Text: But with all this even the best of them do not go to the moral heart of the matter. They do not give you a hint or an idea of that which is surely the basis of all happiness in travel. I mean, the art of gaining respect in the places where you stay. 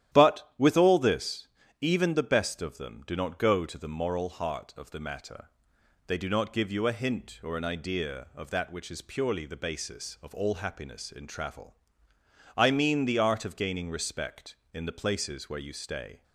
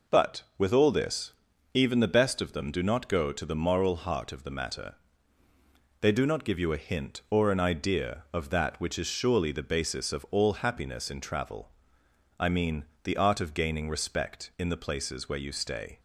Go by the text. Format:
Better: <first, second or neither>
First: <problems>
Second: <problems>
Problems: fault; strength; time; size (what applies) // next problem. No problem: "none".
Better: second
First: starts louder than the rest; strong; until 1.1 s; 11.5 dB // pauses between "this" and "even"; slight; at 1.4 s; 0.34 s long // says "purely" for "surely"; at 9.0 s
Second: pauses between "this" and "even"; at 1.3 s; 0.42 s long